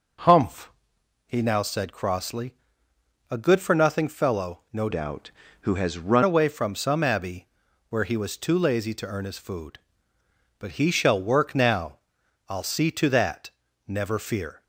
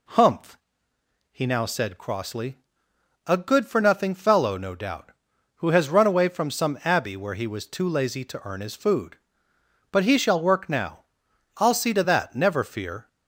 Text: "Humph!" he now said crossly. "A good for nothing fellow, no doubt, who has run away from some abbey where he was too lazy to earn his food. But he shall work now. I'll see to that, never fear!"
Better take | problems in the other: second | changes voice from "doubt" to "run"; from 4.9 to 6.2 s; 1.3 s long // pauses between "abbey" and "where"; at 7.4 s; 0.44 s long

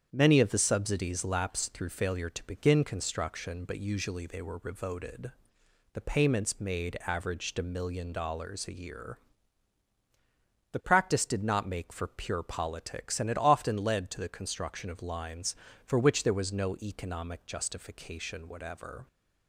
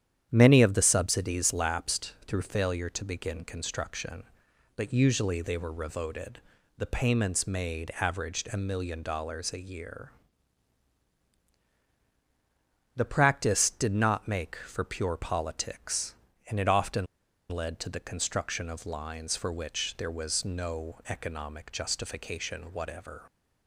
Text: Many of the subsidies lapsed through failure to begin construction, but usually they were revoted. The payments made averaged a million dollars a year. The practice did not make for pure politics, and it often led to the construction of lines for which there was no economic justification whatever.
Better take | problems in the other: first | starts louder than the rest; strong; until 1.3 s; 9.5 dB; strong in the first // pauses between "lapsed" and "through"; slight; at 2.1 s; 0.16 s long // pauses between "often" and "led"; at 17.0 s; 0.44 s long

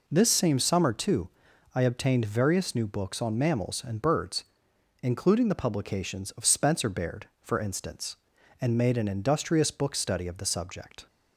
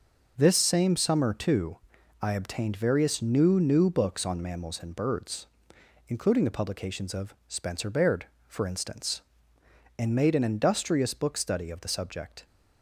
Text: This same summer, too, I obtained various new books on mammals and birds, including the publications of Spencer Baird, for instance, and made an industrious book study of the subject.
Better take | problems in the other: first | says "new" twice; at 3.5 s

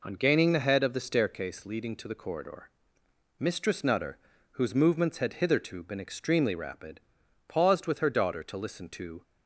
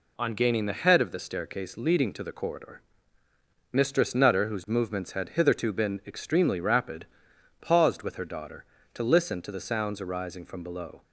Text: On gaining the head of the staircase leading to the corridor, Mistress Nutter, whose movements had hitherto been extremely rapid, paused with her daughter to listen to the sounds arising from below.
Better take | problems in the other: second | stops before "the sounds arising from below"; at 9.2 s

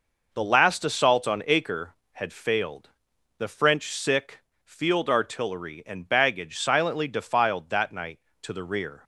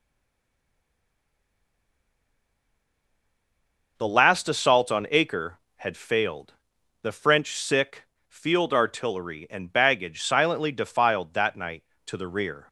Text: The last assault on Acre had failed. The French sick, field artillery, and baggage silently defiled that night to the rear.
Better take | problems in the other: first | stays silent before the first word; strong; until 3.9 s; 3.9 s long

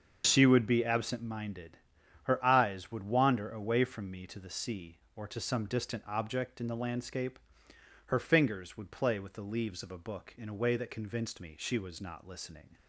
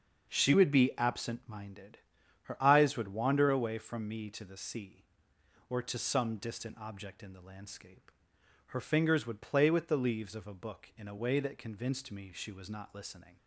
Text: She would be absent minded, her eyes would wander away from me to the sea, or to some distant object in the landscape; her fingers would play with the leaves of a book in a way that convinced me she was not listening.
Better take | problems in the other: second | loses the start of "She"; at 0.2 s; 25 ms // starts louder than the rest; until 1.2 s; 6.5 dB; also in the second

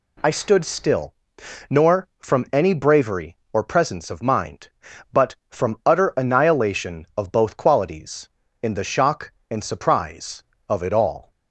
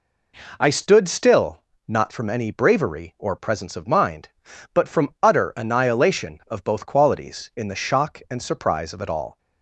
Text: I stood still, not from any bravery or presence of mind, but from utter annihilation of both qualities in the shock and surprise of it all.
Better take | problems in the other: second | says "nor" for "not"; at 1.7 s

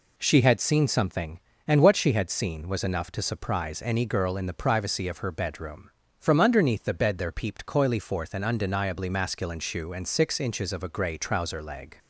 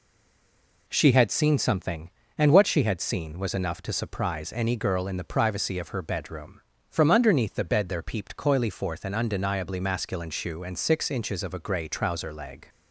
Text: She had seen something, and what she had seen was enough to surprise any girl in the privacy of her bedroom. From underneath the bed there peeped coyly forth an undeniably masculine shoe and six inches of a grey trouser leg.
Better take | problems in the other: first | stays silent before the first word; slight; until 0.8 s; 0.8 s long

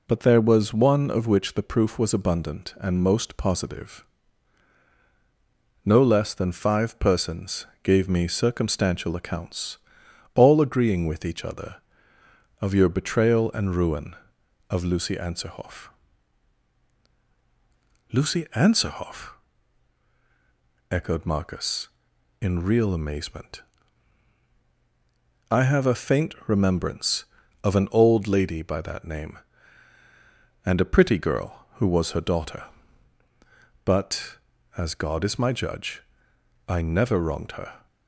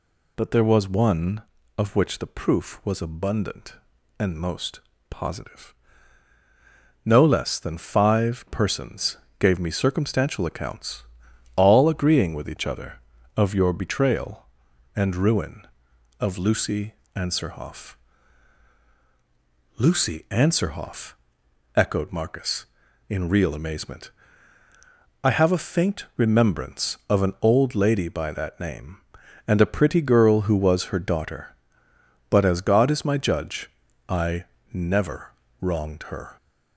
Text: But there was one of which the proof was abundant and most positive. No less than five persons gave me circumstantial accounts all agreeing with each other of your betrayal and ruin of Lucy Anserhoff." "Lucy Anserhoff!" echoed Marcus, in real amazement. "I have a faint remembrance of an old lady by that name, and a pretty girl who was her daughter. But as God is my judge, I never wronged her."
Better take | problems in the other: first | gets louder; slight; throughout; 3 dB // pauses between "most" and "positive"; slight; at 4.8 s; 0.28 s long // pauses between "persons" and "gave"; slight; at 9.1 s; 0.22 s long; slight in the first // pauses between "accounts" and "all"; noticeable; at 11.0 s; 0.54 s long; noticeable in the first // pauses between "Lucy" and "Anserhoff"; slight; at 16.9 s; 0.20 s long // pauses between "I" and "never"; slight; at 34.4 s; 0.28 s long // pauses between "never" and "wronged"; slight; at 35.3 s; 0.30 s long

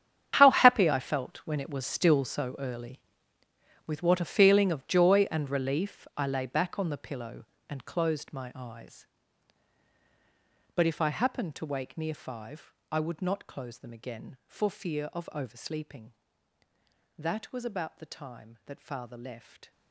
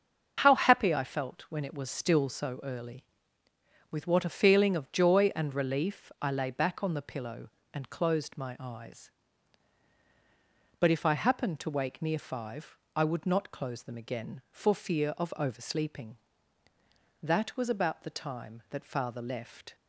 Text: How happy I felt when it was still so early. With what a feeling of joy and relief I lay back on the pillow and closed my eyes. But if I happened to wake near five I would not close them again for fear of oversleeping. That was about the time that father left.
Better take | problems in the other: second | gets quieter; strong; throughout; 15.5 dB // starts louder than the rest; strong; until 1.4 s; 8.5 dB; also in the second // pauses between "five" and "I"; slight; at 12.7 s; 0.18 s long; slight in the second

